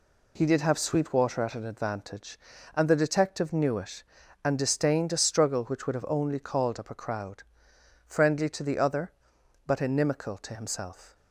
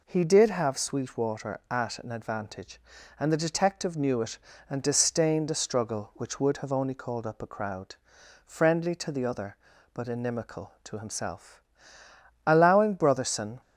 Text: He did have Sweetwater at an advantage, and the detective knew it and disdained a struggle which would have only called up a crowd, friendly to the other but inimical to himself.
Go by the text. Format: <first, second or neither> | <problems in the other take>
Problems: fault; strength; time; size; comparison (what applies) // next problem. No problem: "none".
first | goes on to say "Allowing Brotherson"; noticeable; from 12.4 s on; 1.1 s long